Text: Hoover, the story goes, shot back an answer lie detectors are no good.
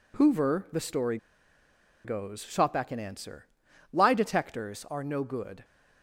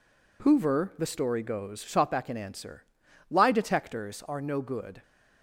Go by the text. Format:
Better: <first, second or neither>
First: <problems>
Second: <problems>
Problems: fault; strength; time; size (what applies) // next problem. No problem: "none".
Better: second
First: pauses between "story" and "goes"; noticeable; at 1.1 s; 0.87 s long // pauses between "answer" and "lie"; noticeable; at 3.4 s; 0.46 s long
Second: pauses between "answer" and "lie"; noticeable; at 2.8 s; 0.46 s long